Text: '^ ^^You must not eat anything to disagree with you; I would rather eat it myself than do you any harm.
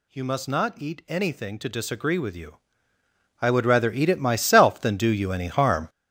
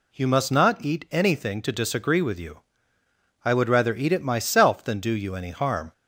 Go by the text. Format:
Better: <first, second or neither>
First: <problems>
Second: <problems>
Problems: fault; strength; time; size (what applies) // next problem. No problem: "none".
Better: second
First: gets louder; strong; throughout; 11 dB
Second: none